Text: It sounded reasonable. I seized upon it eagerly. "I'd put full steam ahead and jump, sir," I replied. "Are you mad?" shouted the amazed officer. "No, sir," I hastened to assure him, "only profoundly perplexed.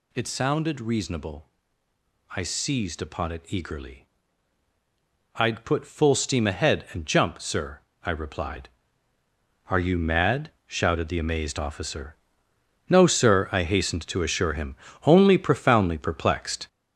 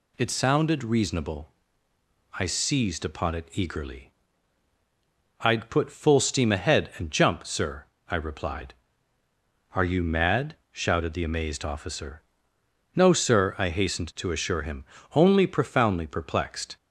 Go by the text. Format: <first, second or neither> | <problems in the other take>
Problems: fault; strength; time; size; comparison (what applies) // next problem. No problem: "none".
second | gets louder; throughout; 6.5 dB